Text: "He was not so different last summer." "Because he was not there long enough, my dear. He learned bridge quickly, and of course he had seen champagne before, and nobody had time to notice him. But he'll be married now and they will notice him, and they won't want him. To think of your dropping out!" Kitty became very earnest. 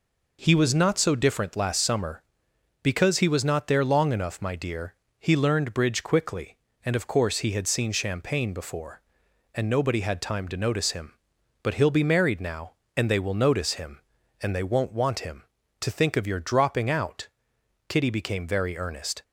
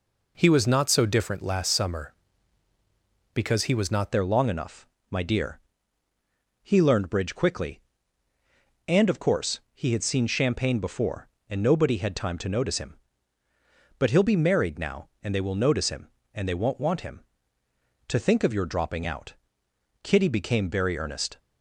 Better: first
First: none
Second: changes voice at "there"; from 4.1 s on; 17.2 s long

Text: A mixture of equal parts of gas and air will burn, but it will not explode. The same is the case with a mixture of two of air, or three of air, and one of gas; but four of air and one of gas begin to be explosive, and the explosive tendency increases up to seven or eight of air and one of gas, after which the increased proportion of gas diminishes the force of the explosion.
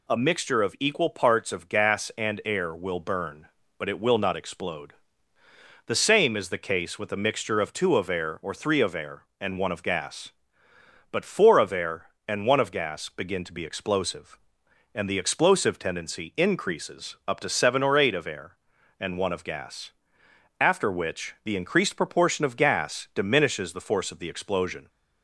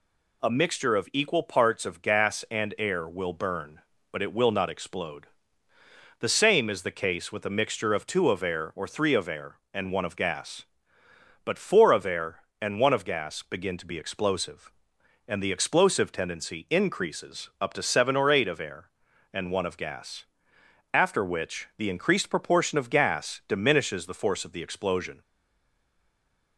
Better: first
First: none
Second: stays silent after the last word; noticeable; from 25.2 s on; 1.3 s long

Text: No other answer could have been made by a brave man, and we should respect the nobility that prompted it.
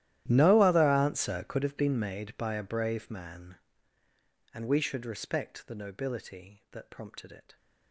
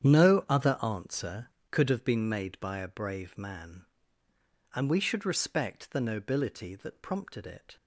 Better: second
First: gets quieter; strong; throughout; 22 dB // starts louder than the rest; strong; until 1.2 s; 13 dB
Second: starts louder than the rest; strong; until 1.1 s; 9 dB

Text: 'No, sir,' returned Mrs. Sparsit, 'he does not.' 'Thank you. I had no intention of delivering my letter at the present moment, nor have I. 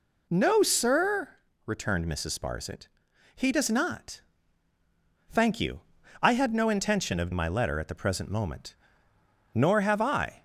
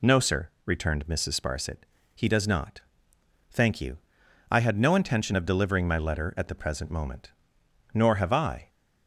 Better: second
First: skips "delivering"; at 7.3 s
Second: none

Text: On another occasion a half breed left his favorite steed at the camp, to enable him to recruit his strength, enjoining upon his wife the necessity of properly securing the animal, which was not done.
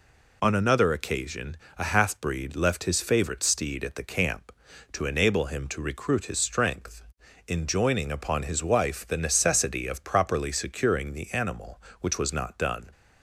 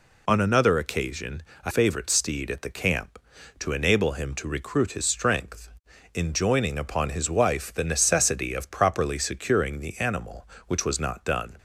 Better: first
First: pauses between "occasion" and "a"; slight; at 1.5 s; 0.23 s long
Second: pauses between "occasion" and "a"; slight; at 1.4 s; 0.24 s long // skips "half breed left his"; at 1.7 s

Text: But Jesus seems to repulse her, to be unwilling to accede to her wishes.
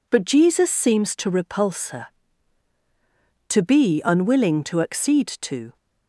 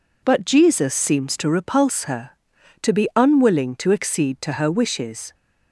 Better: second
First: stops before "her wishes"; at 5.7 s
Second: none

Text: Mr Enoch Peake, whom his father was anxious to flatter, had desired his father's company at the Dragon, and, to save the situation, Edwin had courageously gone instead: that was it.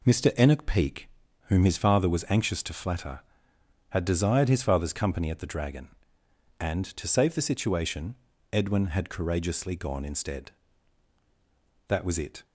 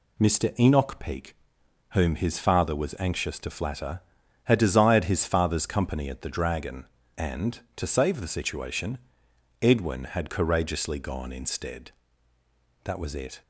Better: neither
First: none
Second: none

